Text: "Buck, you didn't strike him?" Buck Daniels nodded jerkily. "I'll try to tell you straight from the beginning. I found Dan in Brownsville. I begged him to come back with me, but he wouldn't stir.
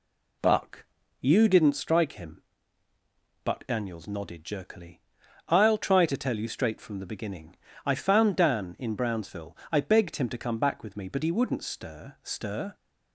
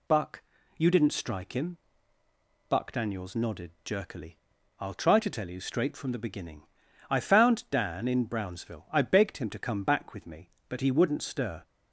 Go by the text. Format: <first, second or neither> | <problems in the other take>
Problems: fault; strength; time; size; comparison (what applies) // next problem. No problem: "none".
second | says "stir" twice; at 12.2 s